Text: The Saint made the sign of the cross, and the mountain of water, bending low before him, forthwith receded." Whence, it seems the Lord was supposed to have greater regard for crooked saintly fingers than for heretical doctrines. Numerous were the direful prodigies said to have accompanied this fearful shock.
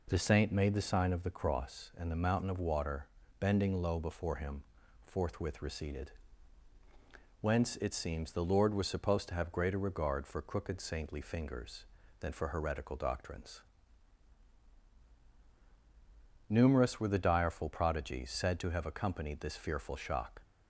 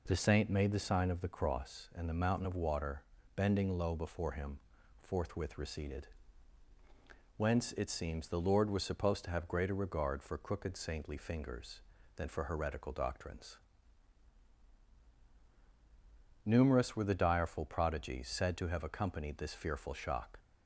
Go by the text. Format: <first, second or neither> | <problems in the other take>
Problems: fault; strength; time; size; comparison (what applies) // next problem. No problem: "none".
neither | none